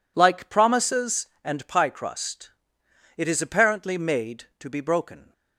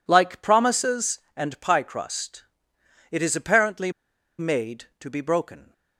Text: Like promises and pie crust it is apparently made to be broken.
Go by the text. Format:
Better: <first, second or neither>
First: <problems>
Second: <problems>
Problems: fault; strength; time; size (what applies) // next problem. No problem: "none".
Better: first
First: pauses between "crust" and "it"; noticeable; at 2.5 s; 0.65 s long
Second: pauses between "crust" and "it"; noticeable; at 2.4 s; 0.66 s long // pauses between "apparently" and "made"; noticeable; at 3.9 s; 0.48 s long